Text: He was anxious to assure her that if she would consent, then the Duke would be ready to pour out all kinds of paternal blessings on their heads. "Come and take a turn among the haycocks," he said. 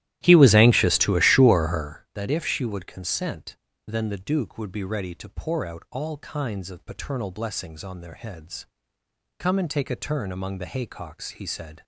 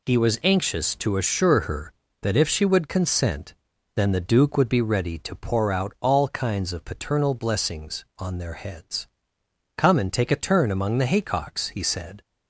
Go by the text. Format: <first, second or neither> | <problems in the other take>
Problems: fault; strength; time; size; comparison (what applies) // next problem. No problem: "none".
second | starts louder than the rest; strong; until 2.0 s; 14.5 dB